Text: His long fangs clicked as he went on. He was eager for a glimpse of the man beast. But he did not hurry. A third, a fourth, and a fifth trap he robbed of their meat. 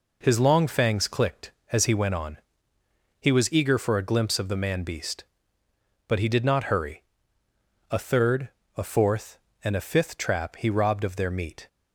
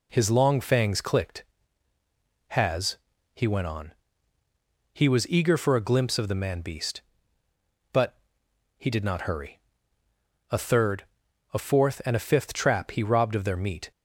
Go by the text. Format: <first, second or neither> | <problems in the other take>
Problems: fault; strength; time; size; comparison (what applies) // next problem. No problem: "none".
first | says "has" for "as"; at 2.4 s // pauses between "But" and "he"; noticeable; at 8.1 s; 0.60 s long